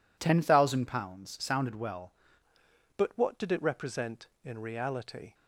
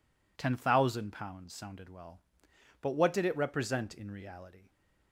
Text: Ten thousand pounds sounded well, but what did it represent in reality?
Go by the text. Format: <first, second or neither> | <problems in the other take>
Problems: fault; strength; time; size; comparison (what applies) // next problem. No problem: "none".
second | changes voice at "but"; from 2.9 s on; 2.4 s long